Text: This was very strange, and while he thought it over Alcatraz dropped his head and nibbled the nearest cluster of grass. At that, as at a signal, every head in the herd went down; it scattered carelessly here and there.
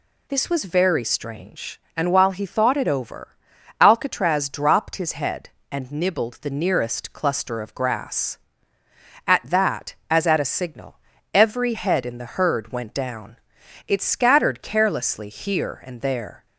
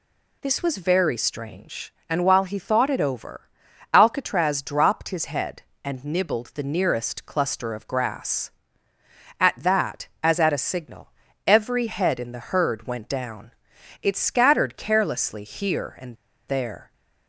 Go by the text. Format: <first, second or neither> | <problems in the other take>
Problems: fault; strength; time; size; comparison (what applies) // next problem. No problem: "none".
first | pauses between "over" and "Alcatraz"; at 3.4 s; 0.44 s long; also in the first // pauses between "and" and "there"; slight; at 16.1 s; 0.34 s long